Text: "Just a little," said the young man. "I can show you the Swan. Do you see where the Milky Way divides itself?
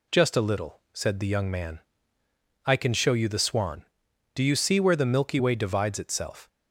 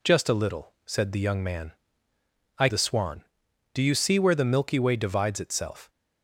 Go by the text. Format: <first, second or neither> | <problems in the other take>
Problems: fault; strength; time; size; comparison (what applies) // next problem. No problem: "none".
first | skips "can show you"; at 2.6 s